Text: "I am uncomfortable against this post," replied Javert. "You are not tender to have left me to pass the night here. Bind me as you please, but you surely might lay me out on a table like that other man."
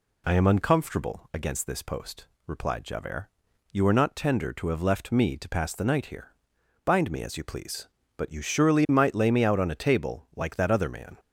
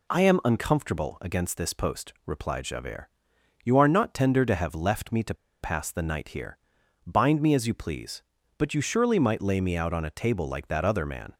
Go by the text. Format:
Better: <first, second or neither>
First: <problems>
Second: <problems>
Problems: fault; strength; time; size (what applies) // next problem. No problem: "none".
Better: first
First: none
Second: pauses between "to" and "pass"; slight; at 5.3 s; 0.27 s long